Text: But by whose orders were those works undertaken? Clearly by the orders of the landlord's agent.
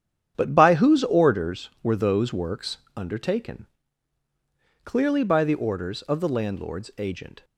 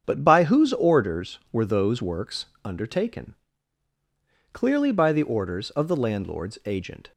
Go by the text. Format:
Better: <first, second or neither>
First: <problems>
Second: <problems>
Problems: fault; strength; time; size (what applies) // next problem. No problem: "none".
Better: second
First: gets quieter; strong; throughout; 10.5 dB // starts louder than the rest; strong; until 1.3 s; 9 dB // pauses between "works" and "undertaken"; slight; at 2.7 s; 0.18 s long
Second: starts louder than the rest; strong; until 1.0 s; 7.5 dB // pauses between "works" and "undertaken"; slight; at 2.4 s; 0.18 s long